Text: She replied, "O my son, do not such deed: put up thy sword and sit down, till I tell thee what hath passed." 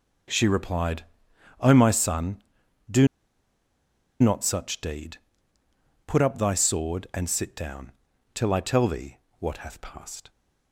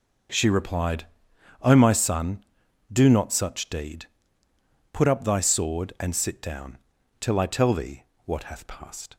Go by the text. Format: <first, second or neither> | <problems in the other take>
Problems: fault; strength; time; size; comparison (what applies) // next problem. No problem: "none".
second | pauses between "do" and "not"; at 3.0 s; 1.1 s long // pauses between "thee" and "what"; slight; at 9.1 s; 0.22 s long; slight in the second